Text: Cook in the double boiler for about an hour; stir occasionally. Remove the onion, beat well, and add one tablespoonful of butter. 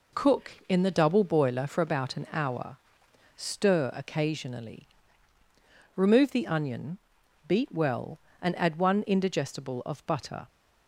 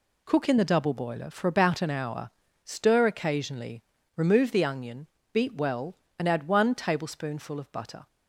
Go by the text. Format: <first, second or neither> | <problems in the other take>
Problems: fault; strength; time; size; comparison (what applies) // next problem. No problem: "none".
second | says "indigestible" for "tablespoonful"; at 9.0 s